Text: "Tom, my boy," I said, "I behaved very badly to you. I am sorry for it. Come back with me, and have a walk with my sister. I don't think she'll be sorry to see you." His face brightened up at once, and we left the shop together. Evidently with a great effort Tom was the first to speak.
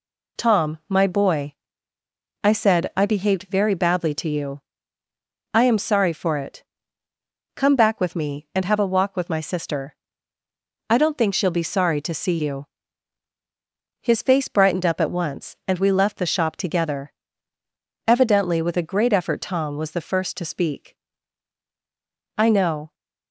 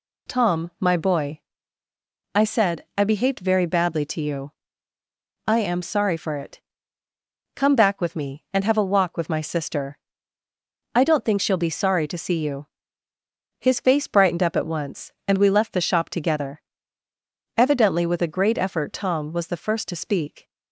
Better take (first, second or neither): second